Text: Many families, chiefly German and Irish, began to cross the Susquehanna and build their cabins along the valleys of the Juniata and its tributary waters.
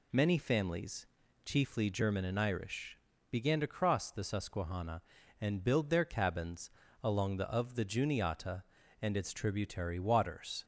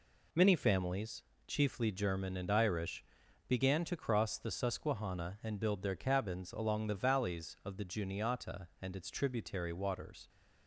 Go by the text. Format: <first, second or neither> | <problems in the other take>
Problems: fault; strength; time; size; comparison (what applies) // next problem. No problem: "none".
second | pauses between "cabins" and "along"; slight; at 6.6 s; 0.34 s long // skips "valleys"; at 7.4 s